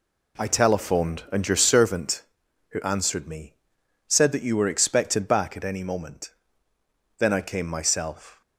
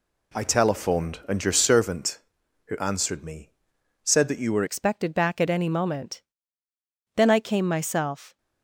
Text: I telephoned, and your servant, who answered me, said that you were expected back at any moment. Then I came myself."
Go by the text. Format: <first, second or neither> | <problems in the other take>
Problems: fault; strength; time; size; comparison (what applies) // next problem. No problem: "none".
first | changes voice at "expected"; from 4.6 s on; 3.7 s long